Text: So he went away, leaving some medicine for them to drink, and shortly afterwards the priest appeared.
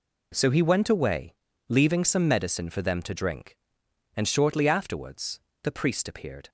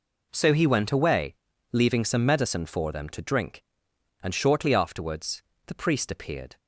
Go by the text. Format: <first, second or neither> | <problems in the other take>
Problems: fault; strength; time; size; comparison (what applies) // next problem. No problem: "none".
neither | pauses between "afterwards" and "the"; slight; the same in both